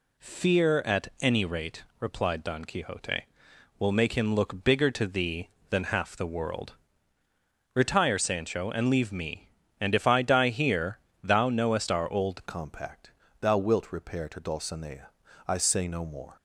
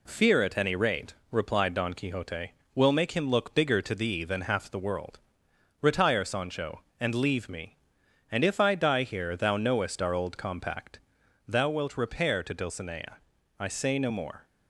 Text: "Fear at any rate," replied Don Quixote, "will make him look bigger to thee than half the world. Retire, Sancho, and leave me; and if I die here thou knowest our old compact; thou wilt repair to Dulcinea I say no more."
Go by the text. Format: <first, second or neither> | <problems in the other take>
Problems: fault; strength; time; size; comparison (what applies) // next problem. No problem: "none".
second | pauses between "here" and "thou"; slight; at 10.9 s; 0.26 s long // changes voice at "compact"; from 12.4 s on; 3.9 s long // pauses between "Dulcinea" and "I"; at 15.0 s; 0.38 s long; also in the second